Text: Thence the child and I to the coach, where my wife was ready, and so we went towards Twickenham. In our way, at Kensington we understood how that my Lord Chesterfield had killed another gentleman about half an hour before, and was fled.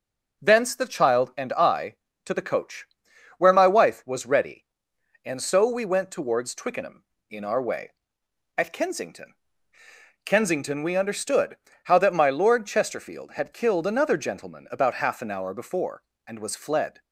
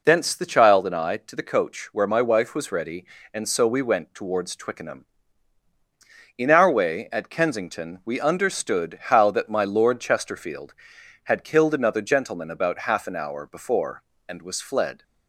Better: second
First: says "Kensington" twice; at 10.2 s // pauses between "understood" and "how"; slight; at 11.5 s; 0.24 s long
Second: none

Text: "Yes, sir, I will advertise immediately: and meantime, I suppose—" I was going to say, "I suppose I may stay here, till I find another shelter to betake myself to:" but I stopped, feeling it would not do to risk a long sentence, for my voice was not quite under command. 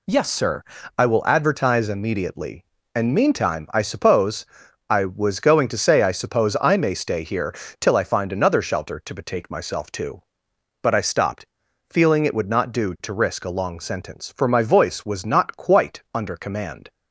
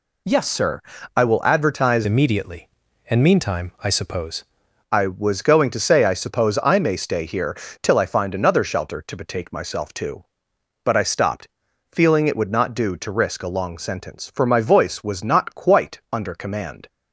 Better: first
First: none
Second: changes voice from "immediately" to "suppose"; from 2.0 to 4.4 s; 2.4 s long

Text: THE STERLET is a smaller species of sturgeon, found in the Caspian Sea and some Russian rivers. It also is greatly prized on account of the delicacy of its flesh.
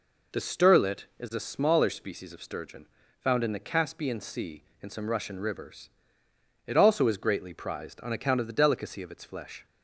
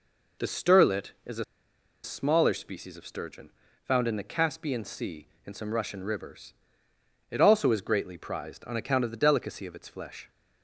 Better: first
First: none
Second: pauses between "a" and "smaller"; noticeable; at 1.4 s; 0.59 s long

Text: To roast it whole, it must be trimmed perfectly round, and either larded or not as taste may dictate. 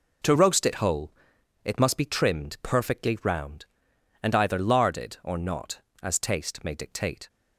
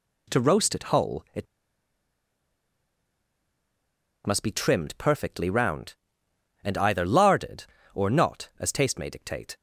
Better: first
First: none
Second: pauses between "it" and "must"; strong; at 1.4 s; 2.8 s long

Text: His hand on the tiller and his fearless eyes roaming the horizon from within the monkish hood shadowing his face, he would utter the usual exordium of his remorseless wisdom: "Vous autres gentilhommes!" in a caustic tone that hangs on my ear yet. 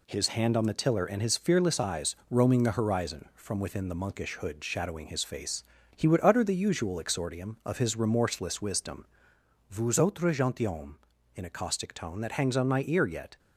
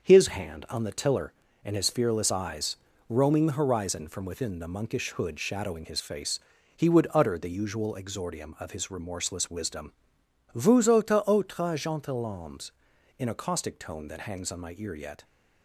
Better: first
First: pauses between "eyes" and "roaming"; slight; at 2.1 s; 0.16 s long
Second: starts louder than the rest; until 1.0 s; 6.5 dB // pauses between "eyes" and "roaming"; slight; at 2.7 s; 0.32 s long // says "autres" twice; at 11.2 s

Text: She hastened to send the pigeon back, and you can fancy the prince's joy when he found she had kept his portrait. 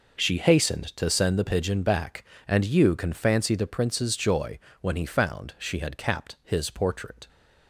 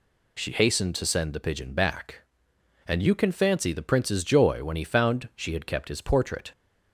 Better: second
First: pauses between "joy" and "when"; slight; at 4.5 s; 0.22 s long // says "capped" for "kept"; at 5.9 s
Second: none

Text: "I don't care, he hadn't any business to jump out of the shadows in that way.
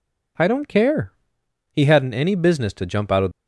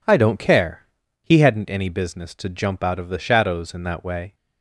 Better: second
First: stops before "the shadows in that way"; at 3.3 s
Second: none

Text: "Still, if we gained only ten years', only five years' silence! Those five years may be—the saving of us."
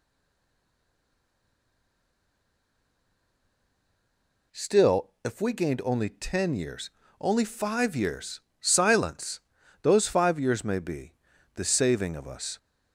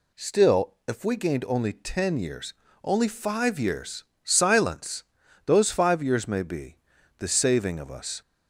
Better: second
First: stays silent before the first word; strong; until 4.5 s; 4.5 s long // pauses between "years" and "silence"; slight; at 8.3 s; 0.20 s long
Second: pauses between "years" and "silence"; slight; at 4.0 s; 0.20 s long

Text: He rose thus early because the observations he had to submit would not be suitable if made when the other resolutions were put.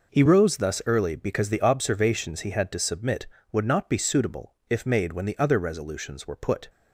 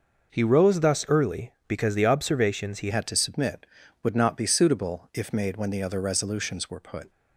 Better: first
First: none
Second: changes voice at "had"; from 2.8 s on; 4.2 s long

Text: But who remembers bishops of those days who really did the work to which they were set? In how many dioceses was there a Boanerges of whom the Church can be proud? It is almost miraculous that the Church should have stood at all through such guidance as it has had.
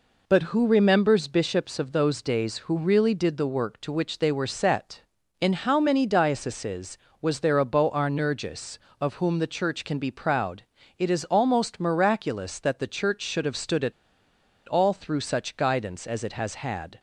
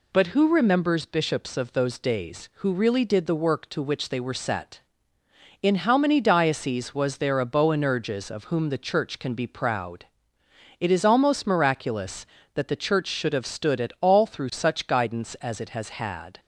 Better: second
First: pauses between "at" and "all"; noticeable; at 13.9 s; 0.74 s long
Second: none

